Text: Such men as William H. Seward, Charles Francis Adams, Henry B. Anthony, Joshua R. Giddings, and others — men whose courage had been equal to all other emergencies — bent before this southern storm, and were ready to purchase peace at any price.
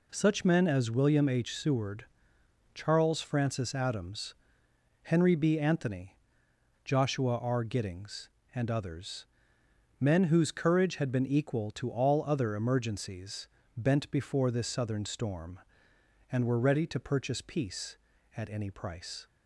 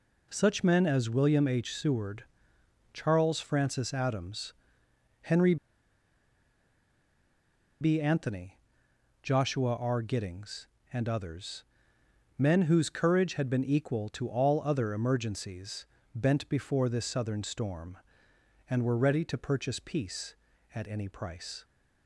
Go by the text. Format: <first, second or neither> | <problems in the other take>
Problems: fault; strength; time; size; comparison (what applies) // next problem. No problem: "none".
first | pauses between "Henry" and "B"; strong; at 5.5 s; 2.2 s long